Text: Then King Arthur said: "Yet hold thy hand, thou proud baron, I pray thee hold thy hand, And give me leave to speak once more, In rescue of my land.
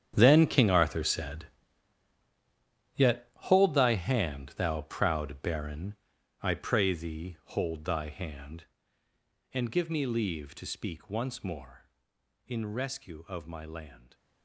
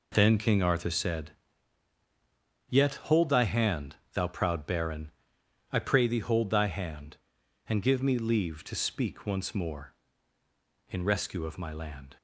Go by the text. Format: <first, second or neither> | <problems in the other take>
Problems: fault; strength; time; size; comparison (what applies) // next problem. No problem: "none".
second | gets quieter; strong; throughout; 14.5 dB